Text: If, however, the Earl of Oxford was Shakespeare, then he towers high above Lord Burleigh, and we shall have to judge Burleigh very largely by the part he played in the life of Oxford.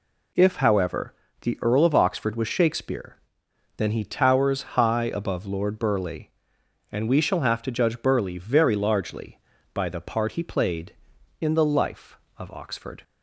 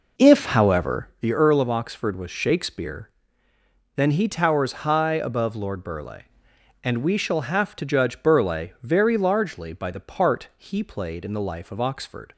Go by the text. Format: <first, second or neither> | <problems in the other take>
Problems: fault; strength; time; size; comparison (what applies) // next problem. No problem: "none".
first | starts louder than the rest; noticeable; until 1.2 s; 4.5 dB